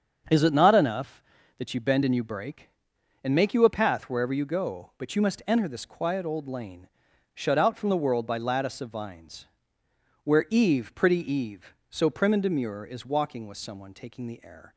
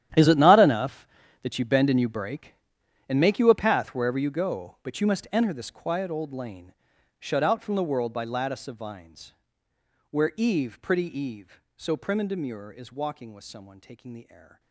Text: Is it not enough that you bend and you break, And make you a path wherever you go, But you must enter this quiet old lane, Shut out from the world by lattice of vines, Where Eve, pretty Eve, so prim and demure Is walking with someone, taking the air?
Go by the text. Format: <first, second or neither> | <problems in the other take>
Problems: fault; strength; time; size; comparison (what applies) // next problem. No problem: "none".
first | gets quieter; strong; throughout; 17.5 dB // starts louder than the rest; strong; until 1.5 s; 11 dB; also in the first